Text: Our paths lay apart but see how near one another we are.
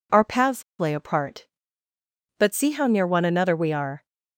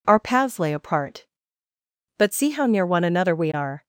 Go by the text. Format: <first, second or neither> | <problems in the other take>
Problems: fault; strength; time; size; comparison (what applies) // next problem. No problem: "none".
second | pauses between "paths" and "lay"; slight; at 0.6 s; 0.16 s long